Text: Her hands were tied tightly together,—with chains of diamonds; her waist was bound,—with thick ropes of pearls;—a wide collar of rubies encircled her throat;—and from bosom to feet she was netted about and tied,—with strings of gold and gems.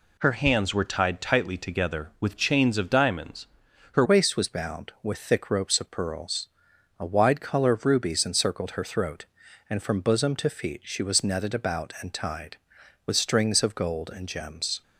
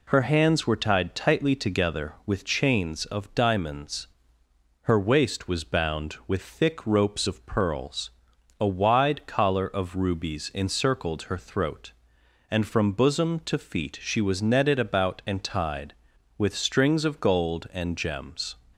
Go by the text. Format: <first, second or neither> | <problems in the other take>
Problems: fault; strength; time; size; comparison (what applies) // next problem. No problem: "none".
second | changes voice at "waist"; from 4.0 s on; 10.8 s long